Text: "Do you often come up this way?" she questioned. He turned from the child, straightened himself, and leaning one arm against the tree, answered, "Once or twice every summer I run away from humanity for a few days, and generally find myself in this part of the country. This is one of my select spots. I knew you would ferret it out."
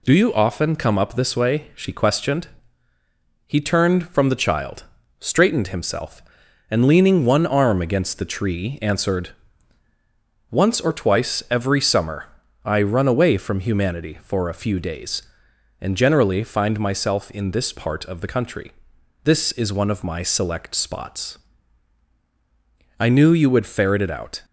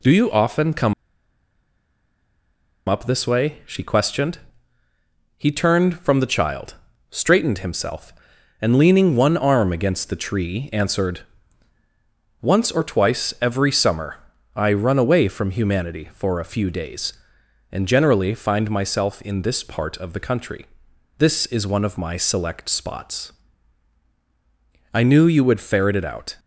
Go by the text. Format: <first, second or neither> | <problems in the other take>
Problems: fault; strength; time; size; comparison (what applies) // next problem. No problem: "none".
first | pauses between "come" and "up"; strong; at 0.9 s; 1.9 s long // pauses between "summer" and "I"; at 14.1 s; 0.40 s long; also in the first